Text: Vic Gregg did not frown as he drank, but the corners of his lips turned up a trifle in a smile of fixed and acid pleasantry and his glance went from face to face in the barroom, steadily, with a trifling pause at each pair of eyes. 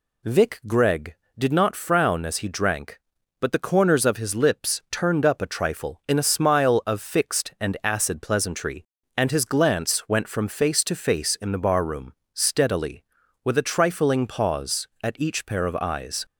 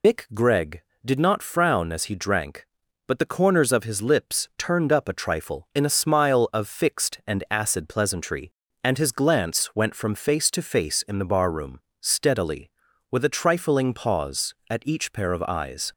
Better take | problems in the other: first | loses the start of "Vic"; at 0.0 s; 130 ms

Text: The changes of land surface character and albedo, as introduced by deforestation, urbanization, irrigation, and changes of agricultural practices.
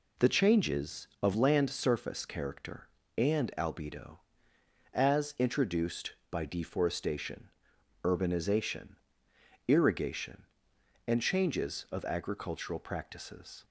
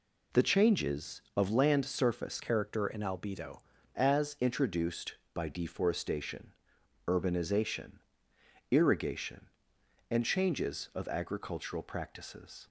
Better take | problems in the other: first | changes voice from "character" to "albedo"; from 2.4 to 3.5 s; 1.1 s long

